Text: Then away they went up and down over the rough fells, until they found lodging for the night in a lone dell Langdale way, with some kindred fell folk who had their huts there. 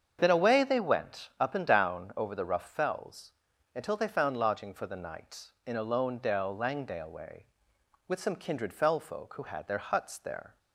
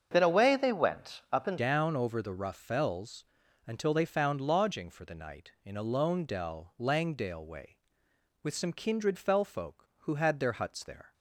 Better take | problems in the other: first | starts louder than the rest; until 1.1 s; 7 dB; strong in the first // changes voice at "down"; from 1.5 s on; 9.6 s long

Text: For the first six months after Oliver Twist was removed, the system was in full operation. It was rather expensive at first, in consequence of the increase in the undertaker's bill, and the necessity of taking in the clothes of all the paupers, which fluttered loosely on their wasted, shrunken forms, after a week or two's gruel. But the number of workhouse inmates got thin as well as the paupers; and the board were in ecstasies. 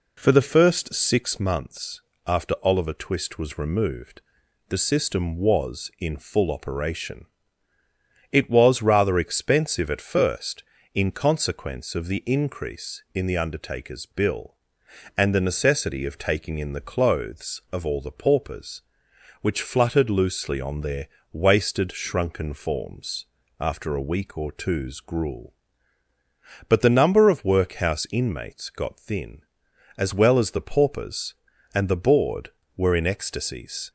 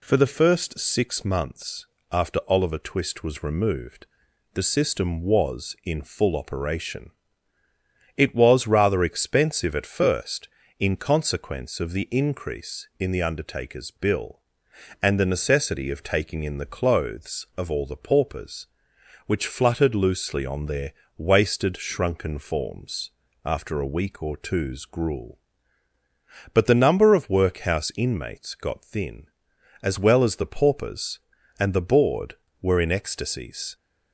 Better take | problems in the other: second | starts louder than the rest; slight; until 1.4 s; 3.5 dB // pauses between "months" and "after"; slight; at 2.0 s; 0.26 s long; slight in the second // pauses between "their" and "wasted"; slight; at 21.0 s; 0.26 s long; slight in the second

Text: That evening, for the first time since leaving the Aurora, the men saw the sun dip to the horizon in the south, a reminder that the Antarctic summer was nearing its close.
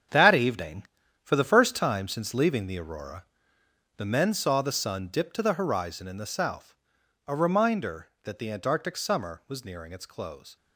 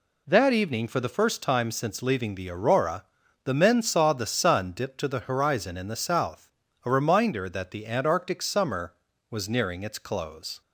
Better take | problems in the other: second | gets quieter; strong; throughout; 9 dB

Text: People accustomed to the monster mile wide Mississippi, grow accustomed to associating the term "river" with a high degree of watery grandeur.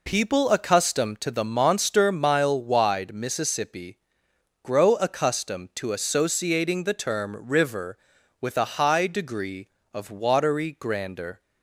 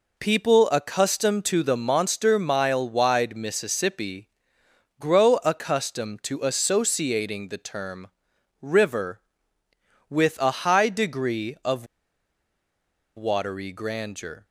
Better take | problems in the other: first | pauses between "term" and "river"; noticeable; at 8.0 s; 0.52 s long // pauses between "of" and "watery"; strong; at 11.8 s; 1.3 s long

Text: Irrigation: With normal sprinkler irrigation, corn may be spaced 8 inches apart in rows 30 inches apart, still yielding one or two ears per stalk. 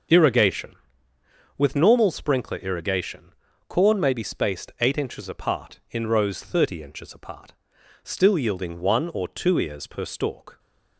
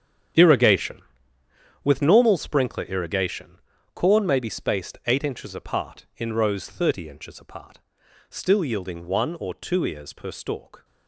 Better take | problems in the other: first | gets quieter; strong; throughout; 13 dB // starts louder than the rest; strong; until 2.1 s; 9 dB; also in the first

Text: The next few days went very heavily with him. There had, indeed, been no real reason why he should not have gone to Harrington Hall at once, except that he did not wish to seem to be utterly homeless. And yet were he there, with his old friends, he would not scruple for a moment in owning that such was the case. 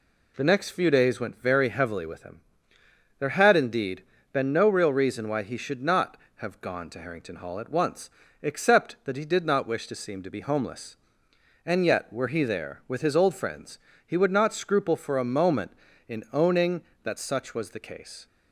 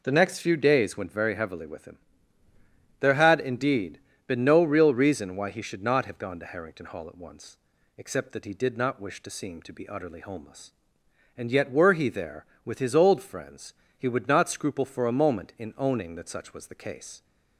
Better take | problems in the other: second | skips "utterly"; at 10.4 s

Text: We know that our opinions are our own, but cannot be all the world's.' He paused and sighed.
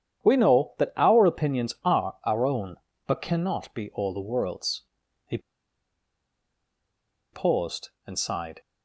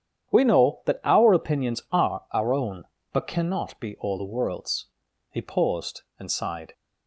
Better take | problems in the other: second | starts louder than the rest; strong; until 1.2 s; 9.5 dB; strong in the second // pauses between "He" and "paused"; strong; at 5.3 s; 1.9 s long

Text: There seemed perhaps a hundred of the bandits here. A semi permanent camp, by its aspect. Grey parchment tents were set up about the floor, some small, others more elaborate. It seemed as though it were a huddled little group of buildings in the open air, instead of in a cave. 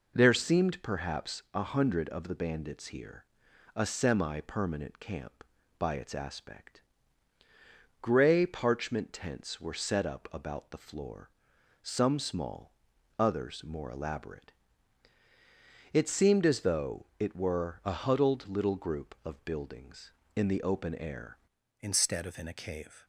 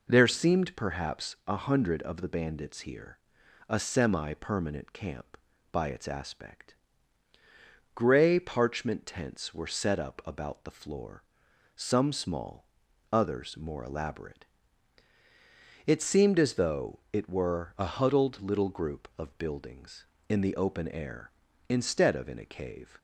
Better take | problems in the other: second | changes voice at "instead"; from 21.8 s on; 1.2 s long

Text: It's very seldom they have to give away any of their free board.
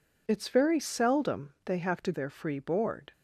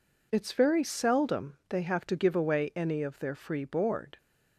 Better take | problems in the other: second | skips "give away any of"; at 2.1 s

